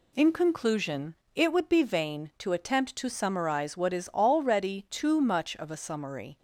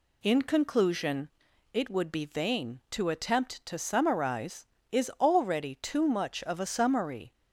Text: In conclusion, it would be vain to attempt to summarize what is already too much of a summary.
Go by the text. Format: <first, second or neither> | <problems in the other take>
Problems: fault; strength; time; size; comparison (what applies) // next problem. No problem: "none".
first | skips "what"; at 4.7 s